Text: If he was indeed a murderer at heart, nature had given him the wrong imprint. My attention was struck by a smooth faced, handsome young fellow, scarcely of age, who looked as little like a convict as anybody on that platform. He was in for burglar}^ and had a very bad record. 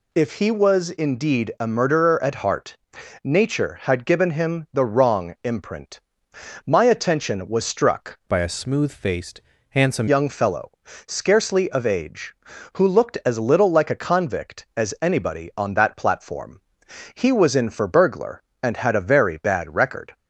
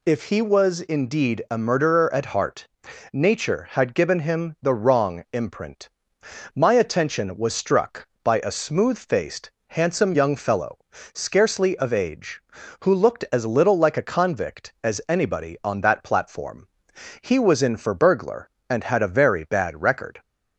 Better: second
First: changes voice from "by" to "handsome"; from 8.2 to 10.0 s; 1.8 s long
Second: none

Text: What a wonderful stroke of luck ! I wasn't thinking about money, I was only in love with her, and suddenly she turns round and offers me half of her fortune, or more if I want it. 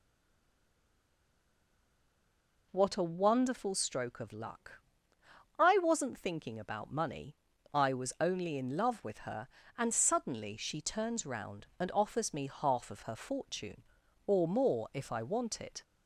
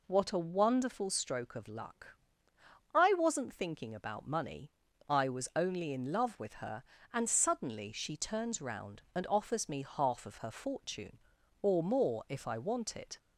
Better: second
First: stays silent before the first word; strong; until 2.7 s; 2.7 s long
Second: none

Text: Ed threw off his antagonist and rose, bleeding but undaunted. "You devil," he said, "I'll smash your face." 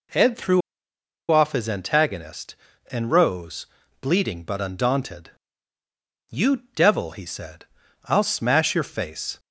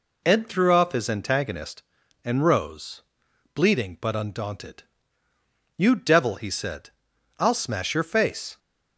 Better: second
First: pauses between "threw" and "off"; noticeable; at 0.6 s; 0.70 s long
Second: none

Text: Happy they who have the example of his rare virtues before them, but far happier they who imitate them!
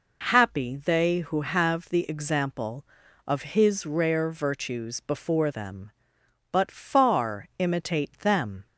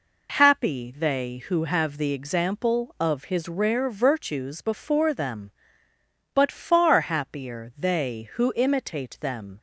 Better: second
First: skips "happier they who"; at 7.5 s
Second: none

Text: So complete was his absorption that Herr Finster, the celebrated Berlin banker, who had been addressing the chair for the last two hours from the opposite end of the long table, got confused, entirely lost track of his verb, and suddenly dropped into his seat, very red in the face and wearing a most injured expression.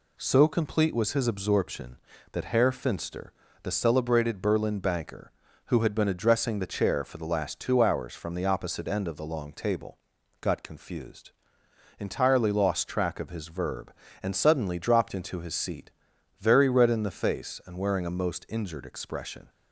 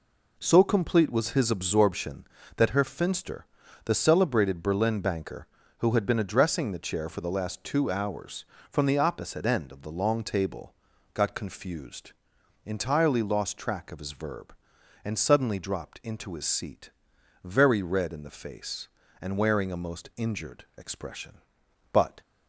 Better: first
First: none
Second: goes on to say "But"; slight; from 21.9 s on; 0.28 s long

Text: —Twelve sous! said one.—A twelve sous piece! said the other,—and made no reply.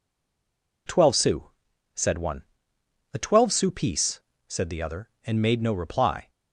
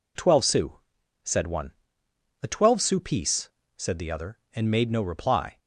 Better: second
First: stays silent before the first word; slight; until 0.8 s; 0.8 s long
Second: none

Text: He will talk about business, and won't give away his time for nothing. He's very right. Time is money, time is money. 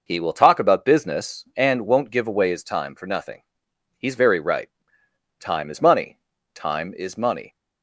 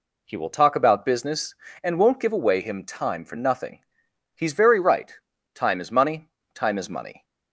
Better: first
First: none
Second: says "him" for "his"; at 2.6 s

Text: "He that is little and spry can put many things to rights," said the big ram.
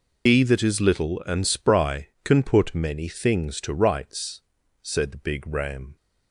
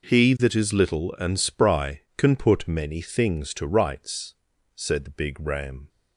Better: second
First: loses the start of "He"; at 0.2 s; 125 ms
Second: none

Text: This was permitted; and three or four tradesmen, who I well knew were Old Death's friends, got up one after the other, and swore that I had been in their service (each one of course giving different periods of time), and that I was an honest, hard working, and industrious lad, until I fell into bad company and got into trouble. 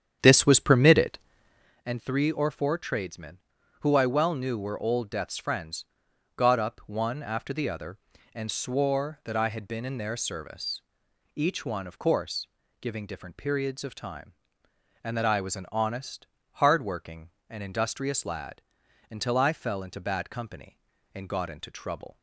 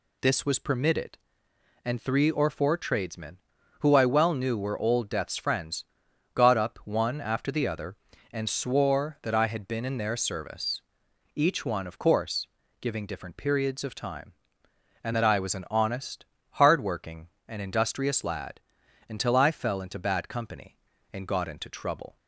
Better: second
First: starts louder than the rest; strong; until 1.8 s; 9 dB // pauses between "course" and "giving"; slight; at 12.4 s; 0.34 s long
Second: pauses between "course" and "giving"; slight; at 12.4 s; 0.34 s long

